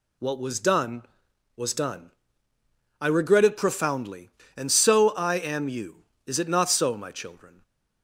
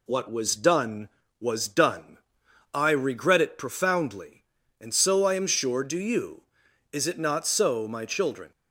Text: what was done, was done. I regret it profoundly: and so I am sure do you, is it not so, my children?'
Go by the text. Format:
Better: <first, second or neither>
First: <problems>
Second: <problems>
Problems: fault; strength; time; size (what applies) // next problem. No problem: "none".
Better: second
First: skips "sure do"; at 5.6 s // stays silent after the last word; slight; from 7.5 s on; 0.5 s long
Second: none